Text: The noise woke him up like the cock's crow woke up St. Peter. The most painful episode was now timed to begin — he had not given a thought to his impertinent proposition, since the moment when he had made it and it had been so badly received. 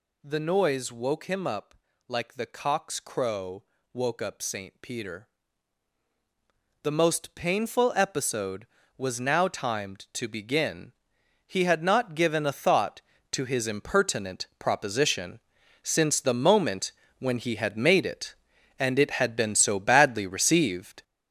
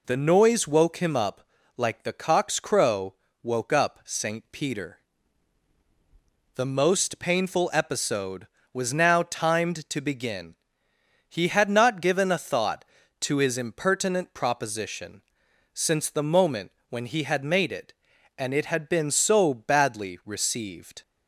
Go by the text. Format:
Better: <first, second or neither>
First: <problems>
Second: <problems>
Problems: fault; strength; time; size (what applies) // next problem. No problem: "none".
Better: second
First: gets louder; strong; throughout; 7.5 dB // pauses between "up" and "like"; slight; at 1.7 s; 0.34 s long // pauses between "crow" and "woke"; slight; at 3.6 s; 0.30 s long // pauses between "moment" and "when"; slight; at 16.9 s; 0.26 s long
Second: pauses between "up" and "like"; slight; at 1.4 s; 0.34 s long // pauses between "crow" and "woke"; slight; at 3.1 s; 0.28 s long // pauses between "moment" and "when"; slight; at 16.6 s; 0.20 s long